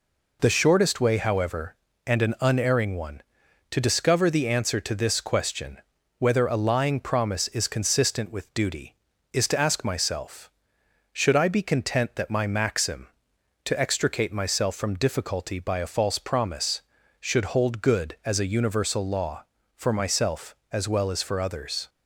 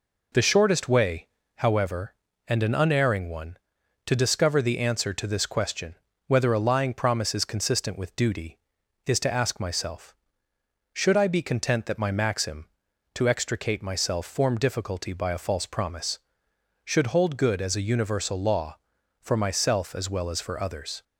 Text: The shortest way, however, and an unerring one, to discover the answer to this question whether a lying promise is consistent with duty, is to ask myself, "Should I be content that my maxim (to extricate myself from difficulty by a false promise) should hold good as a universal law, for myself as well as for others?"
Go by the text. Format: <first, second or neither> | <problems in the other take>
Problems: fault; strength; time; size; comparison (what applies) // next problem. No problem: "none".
first | pauses between "question" and "whether"; slight; at 5.9 s; 0.34 s long; also in the first // says "form" for "from"; at 14.2 s